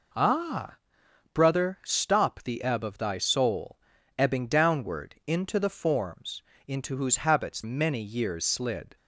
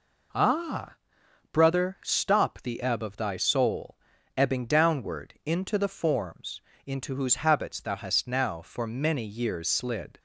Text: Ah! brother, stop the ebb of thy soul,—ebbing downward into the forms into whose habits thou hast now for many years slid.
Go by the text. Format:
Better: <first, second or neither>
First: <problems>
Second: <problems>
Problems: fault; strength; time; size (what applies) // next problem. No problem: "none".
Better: second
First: pauses between "forms" and "into"; slight; at 6.4 s; 0.26 s long // skips "thou hast now for"; at 7.6 s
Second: pauses between "forms" and "into"; slight; at 6.6 s; 0.26 s long